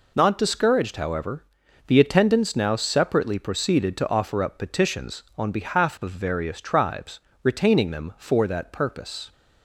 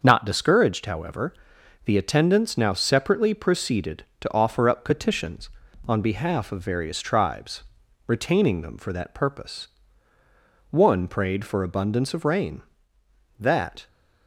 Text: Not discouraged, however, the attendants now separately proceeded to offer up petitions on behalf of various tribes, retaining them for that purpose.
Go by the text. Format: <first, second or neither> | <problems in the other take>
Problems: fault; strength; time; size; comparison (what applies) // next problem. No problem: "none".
first | starts louder than the rest; until 1.0 s; 6.5 dB // goes on to say "One prayed for abundance of rain that"; strong; from 10.7 s on; 3.1 s long